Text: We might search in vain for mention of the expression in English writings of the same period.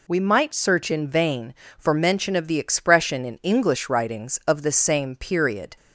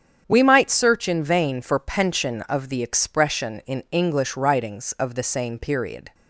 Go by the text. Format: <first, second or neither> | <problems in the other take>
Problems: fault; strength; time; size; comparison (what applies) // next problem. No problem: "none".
first | starts louder than the rest; strong; until 1.2 s; 8.5 dB // says "pension" for "mention"; at 1.7 s